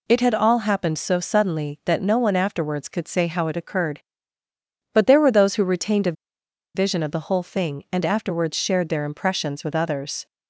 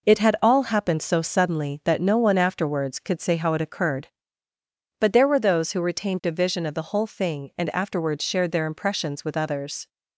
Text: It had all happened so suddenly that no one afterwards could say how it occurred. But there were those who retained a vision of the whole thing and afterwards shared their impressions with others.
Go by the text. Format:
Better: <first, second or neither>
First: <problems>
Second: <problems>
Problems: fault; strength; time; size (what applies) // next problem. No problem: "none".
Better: second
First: pauses between "a" and "vision"; noticeable; at 6.1 s; 0.62 s long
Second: none